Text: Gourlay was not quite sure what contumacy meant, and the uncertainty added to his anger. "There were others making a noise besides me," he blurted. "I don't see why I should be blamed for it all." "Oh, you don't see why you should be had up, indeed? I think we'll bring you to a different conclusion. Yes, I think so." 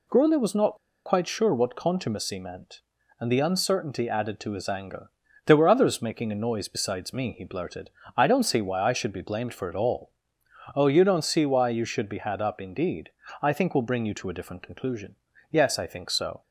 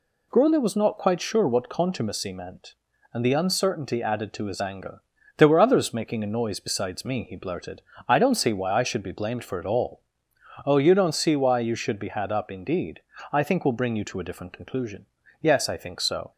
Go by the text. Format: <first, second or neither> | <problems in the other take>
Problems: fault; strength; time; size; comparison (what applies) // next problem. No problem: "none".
second | pauses between "not" and "quite"; slight; at 0.7 s; 0.28 s long